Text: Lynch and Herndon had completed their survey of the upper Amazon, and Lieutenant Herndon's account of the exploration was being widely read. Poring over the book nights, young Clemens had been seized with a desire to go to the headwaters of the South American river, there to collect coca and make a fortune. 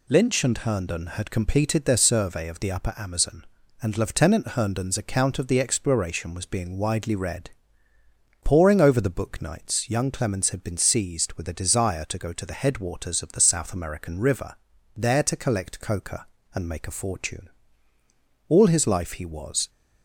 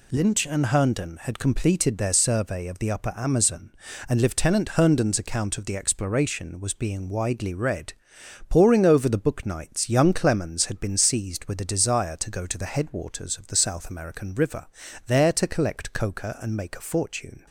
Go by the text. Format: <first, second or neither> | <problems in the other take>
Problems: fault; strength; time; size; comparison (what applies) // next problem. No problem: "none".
second | goes on to say "All his life he was"; noticeable; from 18.4 s on; 1.2 s long